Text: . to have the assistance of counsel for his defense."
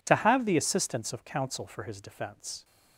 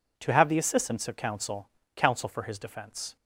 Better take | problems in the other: first | says "counsel" twice; at 1.9 s

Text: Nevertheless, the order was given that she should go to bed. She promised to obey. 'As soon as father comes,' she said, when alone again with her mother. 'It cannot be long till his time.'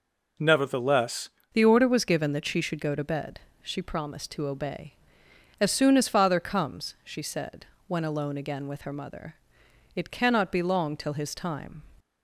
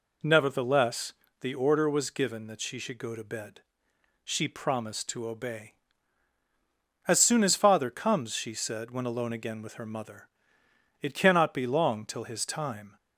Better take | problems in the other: second | changes voice at "the"; from 1.5 s on; 10.3 s long

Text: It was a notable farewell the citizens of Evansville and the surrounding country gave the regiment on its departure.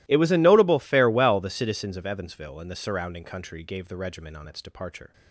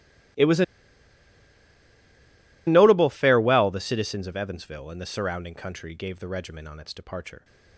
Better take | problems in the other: first | starts louder than the rest; strong; until 3.4 s; 18.5 dB; strong in the first // pauses between "a" and "notable"; strong; at 0.6 s; 2.0 s long

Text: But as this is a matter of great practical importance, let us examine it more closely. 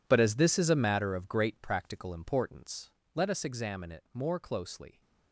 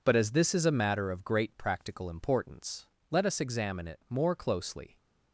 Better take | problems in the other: second | gets quieter; strong; throughout; 15 dB

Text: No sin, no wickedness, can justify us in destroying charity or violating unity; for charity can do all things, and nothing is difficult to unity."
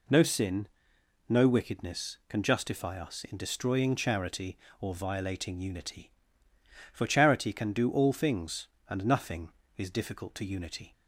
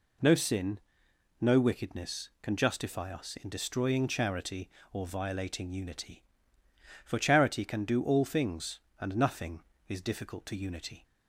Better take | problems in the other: neither | none

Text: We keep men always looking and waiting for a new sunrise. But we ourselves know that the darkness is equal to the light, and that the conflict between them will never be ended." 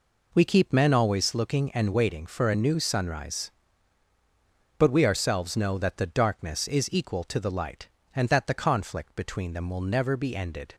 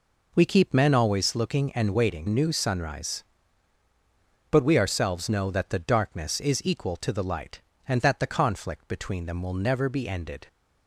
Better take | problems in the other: first | skips "for a"; at 2.2 s

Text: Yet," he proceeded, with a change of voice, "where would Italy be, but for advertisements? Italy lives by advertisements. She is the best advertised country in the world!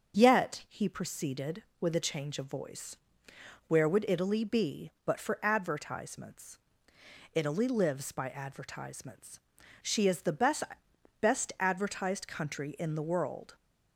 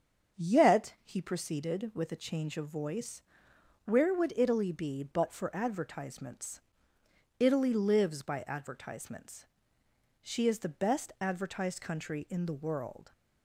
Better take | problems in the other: second | starts louder than the rest; until 1.2 s; 6.5 dB; strong in the second // says "best" twice; at 11.1 s

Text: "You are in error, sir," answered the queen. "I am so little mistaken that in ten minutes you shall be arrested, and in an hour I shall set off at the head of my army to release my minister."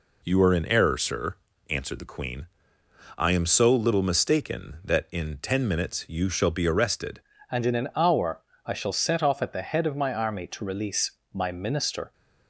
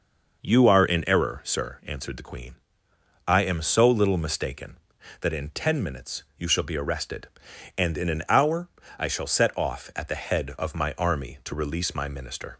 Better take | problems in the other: second | changes voice at "and"; from 7.5 s on; 4.6 s long // pauses between "hour" and "I"; slight; at 8.4 s; 0.24 s long; slight in the second // pauses between "release" and "my"; slight; at 11.1 s; 0.20 s long

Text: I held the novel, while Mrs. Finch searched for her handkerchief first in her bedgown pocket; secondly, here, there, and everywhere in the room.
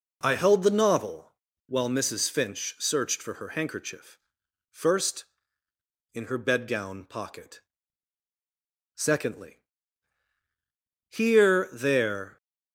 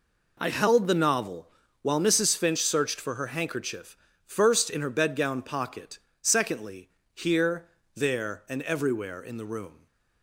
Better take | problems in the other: second | pauses between "handkerchief" and "first"; noticeable; at 4.1 s; 0.52 s long; slight in the second // stops before "and everywhere in the room"; at 12.3 s

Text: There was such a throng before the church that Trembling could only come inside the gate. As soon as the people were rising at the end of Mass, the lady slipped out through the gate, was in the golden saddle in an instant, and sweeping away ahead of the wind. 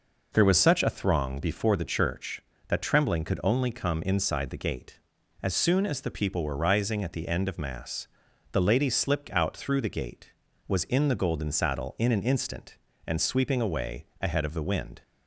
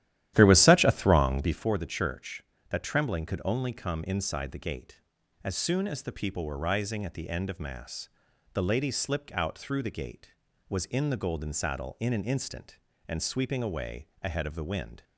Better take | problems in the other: first | starts louder than the rest; strong; until 1.7 s; 12.5 dB // pauses between "away" and "ahead"; slight; at 14.0 s; 0.16 s long; slight in the first

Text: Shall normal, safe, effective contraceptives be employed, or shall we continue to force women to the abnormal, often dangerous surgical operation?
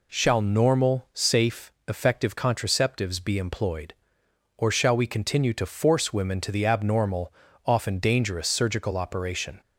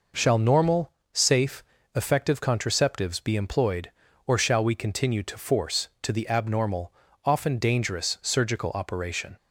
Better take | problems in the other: first | skips "women"; at 5.9 s

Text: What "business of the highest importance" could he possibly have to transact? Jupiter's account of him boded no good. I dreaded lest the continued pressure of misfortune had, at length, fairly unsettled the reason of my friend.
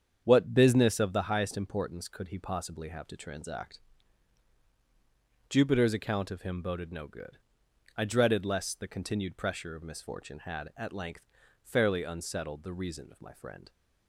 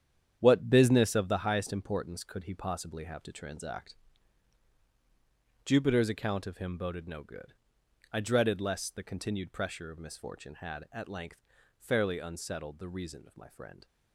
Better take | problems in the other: first | gets quieter; strong; throughout; 9.5 dB // starts louder than the rest; strong; until 1.4 s; 9 dB; strong in the first

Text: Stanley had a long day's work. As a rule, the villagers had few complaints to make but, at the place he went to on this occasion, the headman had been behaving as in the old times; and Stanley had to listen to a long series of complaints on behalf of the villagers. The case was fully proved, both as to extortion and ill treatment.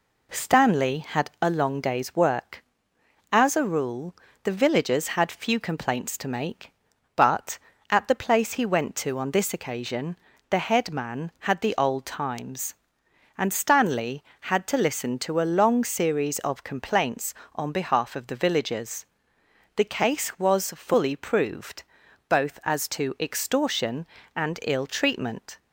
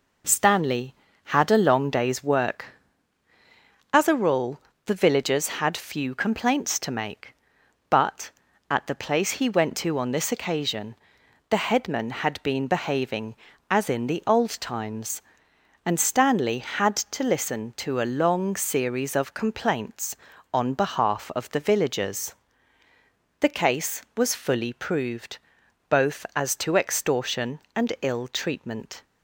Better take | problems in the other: second | skips "been behaving as in"; at 11.6 s

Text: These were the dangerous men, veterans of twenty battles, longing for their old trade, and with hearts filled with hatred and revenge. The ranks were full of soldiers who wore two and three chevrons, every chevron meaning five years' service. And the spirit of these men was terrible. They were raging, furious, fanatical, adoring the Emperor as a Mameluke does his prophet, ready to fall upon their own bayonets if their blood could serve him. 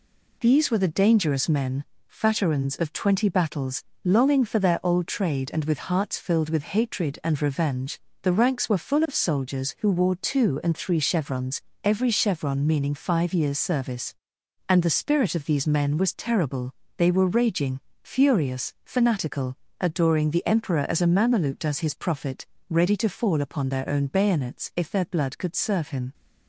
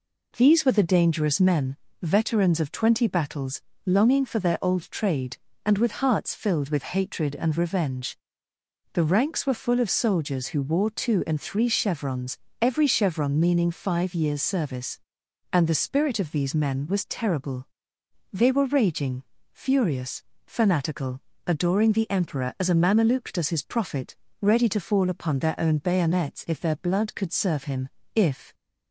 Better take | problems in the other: first | goes on to say "If"; slight; from 28.1 s on; 0.40 s long

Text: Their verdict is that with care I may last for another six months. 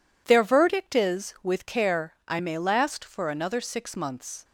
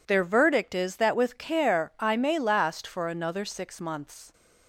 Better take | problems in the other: second | skips "that"; at 1.3 s

